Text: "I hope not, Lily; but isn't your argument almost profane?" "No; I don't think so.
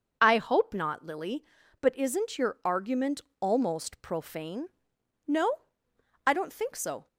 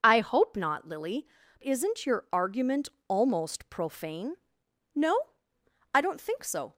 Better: first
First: pauses between "argument" and "almost"; slight; at 3.1 s; 0.22 s long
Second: skips "but"; at 1.4 s // pauses between "argument" and "almost"; slight; at 2.8 s; 0.22 s long

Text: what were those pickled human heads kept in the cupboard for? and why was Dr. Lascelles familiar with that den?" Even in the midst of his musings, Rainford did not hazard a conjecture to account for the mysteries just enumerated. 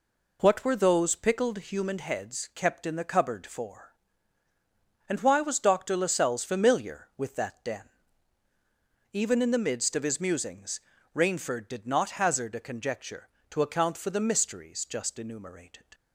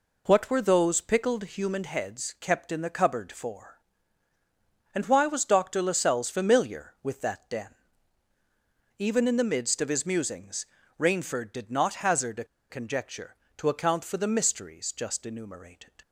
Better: first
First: none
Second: pauses between "a" and "conjecture"; slight; at 12.4 s; 0.25 s long

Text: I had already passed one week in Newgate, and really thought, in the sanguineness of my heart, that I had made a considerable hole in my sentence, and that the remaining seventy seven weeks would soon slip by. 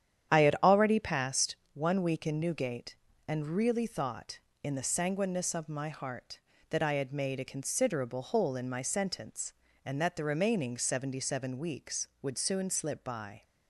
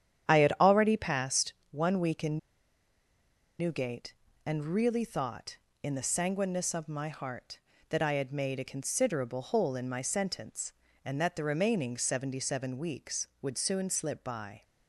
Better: first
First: starts louder than the rest; strong; until 1.4 s; 9.5 dB // pauses between "passed" and "one"; slight; at 1.5 s; 0.18 s long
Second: starts louder than the rest; strong; until 1.3 s; 9.5 dB // pauses between "passed" and "one"; slight; at 1.5 s; 0.18 s long // pauses between "in" and "Newgate"; at 2.3 s; 1.2 s long

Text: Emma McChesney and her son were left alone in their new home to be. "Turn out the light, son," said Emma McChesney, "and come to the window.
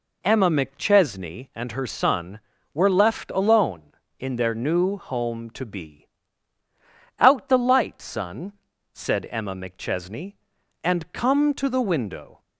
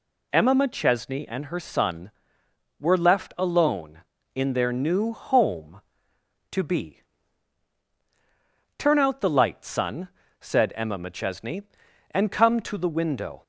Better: second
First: skips "Turn"; at 6.6 s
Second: none

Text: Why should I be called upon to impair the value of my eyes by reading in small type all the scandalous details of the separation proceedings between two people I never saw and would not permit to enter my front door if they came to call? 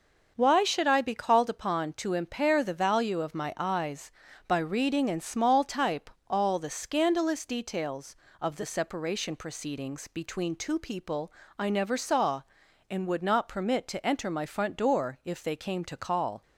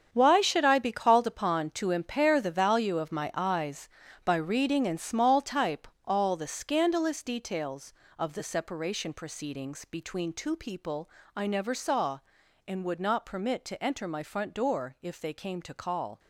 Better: first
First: starts louder than the rest; noticeable; until 1.3 s; 6 dB // pauses between "type" and "all"; slight; at 6.0 s; 0.18 s long // pauses between "people" and "I"; slight; at 11.3 s; 0.24 s long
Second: gets quieter; strong; throughout; 11.5 dB // starts louder than the rest; strong; until 1.1 s; 7.5 dB // pauses between "type" and "all"; slight; at 5.8 s; 0.18 s long // pauses between "people" and "I"; slight; at 11.0 s; 0.24 s long

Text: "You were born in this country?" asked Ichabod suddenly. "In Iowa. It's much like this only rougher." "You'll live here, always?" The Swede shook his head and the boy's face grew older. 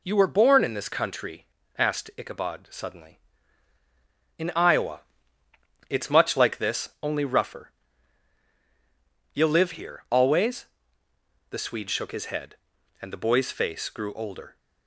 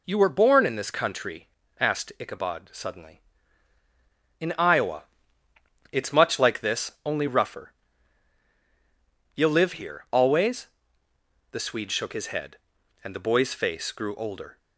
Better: neither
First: none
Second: none

